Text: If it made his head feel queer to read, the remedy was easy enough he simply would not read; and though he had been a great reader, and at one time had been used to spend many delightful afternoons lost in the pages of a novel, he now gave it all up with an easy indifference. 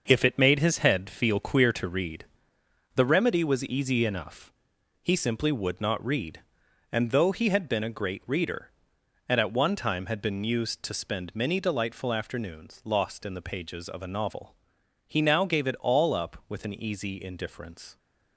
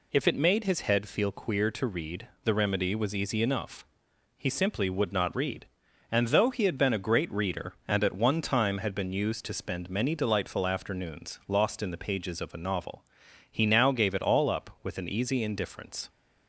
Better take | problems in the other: second | gets quieter; strong; throughout; 7.5 dB // pauses between "enough" and "he"; noticeable; at 4.5 s; 0.50 s long; noticeable in the second

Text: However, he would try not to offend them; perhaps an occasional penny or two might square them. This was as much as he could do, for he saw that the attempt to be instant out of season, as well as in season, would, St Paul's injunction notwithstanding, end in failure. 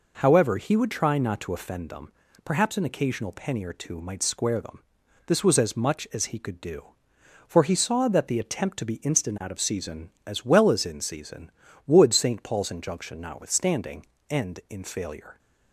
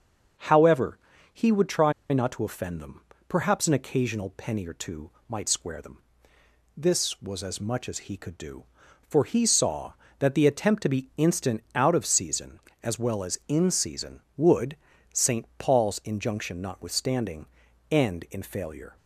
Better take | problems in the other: first | starts louder than the rest; until 1.7 s; 6.5 dB // pauses between "try" and "not"; slight; at 1.9 s; 0.19 s long // pauses between "two" and "might"; slight; at 5.1 s; 0.18 s long

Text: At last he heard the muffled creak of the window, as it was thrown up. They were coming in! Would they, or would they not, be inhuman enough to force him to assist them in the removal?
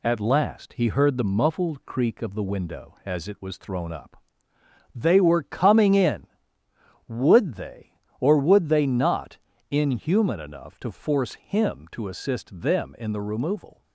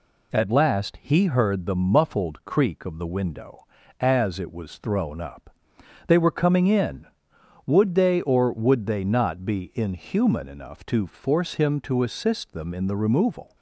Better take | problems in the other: second | skips "be"; at 9.5 s

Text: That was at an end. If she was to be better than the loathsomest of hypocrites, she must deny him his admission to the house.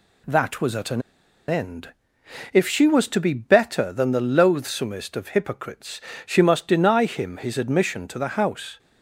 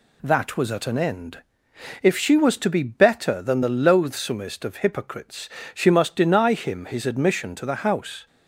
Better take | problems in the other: second | pauses between "an" and "end"; noticeable; at 1.0 s; 0.46 s long

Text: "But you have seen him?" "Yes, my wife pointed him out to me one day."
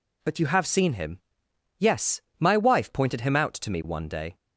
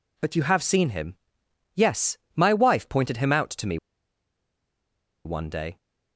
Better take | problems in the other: first | pauses between "me" and "one"; strong; at 3.7 s; 1.4 s long

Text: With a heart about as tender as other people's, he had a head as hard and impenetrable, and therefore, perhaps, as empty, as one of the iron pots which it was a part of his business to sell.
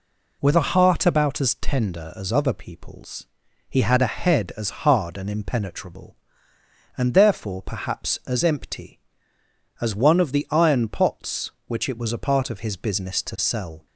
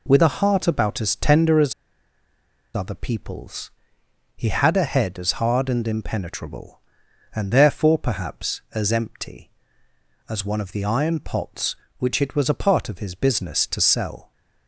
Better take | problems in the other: first | pauses between "as" and "other"; at 1.7 s; 1.0 s long

